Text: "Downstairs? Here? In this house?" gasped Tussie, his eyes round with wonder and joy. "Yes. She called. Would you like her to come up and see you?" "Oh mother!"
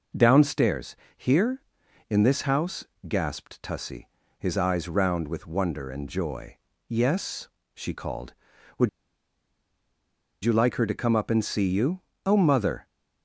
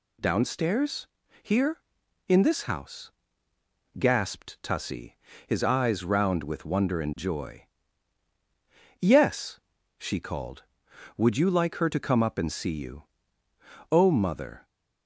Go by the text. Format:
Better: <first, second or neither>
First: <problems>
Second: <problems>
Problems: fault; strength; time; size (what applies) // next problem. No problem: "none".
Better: second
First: pauses between "Would" and "you"; strong; at 8.8 s; 1.5 s long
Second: none